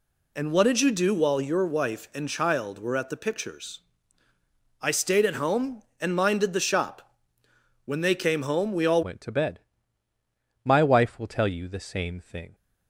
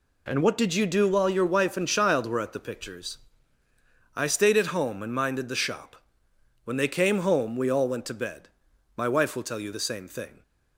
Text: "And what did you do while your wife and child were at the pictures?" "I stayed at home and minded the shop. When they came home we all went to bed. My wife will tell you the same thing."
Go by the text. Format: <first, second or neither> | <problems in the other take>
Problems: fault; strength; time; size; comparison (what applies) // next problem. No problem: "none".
second | changes voice at "went"; from 9.0 s on; 3.5 s long